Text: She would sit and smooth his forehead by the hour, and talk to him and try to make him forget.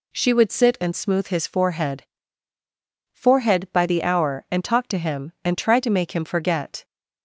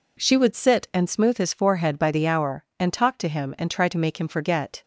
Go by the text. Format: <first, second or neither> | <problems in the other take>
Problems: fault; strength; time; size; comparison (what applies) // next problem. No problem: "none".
second | says "forehead" twice; at 3.1 s